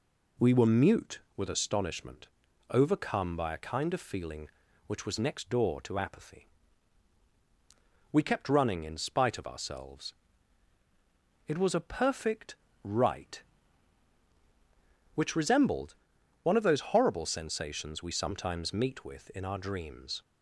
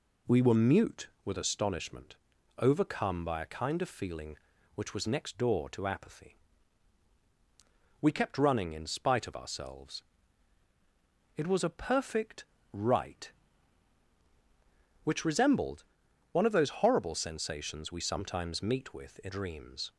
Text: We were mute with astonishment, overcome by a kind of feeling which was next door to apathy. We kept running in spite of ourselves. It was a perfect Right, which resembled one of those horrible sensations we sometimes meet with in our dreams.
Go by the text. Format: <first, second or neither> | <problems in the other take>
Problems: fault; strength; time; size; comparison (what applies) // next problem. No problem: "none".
first | pauses between "perfect" and "Right"; slight; at 12.4 s; 0.28 s long; slight in the first // pauses between "resembled" and "one"; noticeable; at 15.8 s; 0.48 s long; noticeable in the first // skips "our"; at 19.2 s